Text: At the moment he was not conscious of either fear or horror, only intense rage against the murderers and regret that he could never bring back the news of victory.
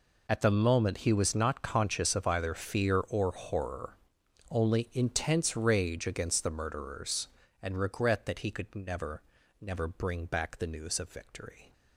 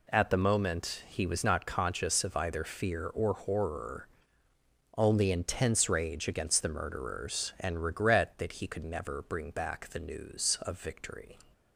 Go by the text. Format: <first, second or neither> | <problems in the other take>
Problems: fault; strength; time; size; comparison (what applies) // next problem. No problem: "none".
second | says "never" twice; at 9.6 s